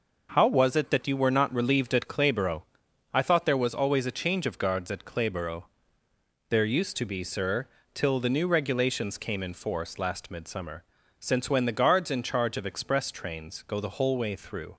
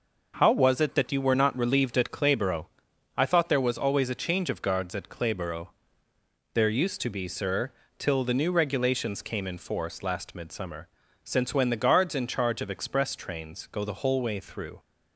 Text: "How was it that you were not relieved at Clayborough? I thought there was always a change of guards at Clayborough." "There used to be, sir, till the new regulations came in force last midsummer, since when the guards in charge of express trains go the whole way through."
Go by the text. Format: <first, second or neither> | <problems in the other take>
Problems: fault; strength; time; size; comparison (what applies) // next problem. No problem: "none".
neither | none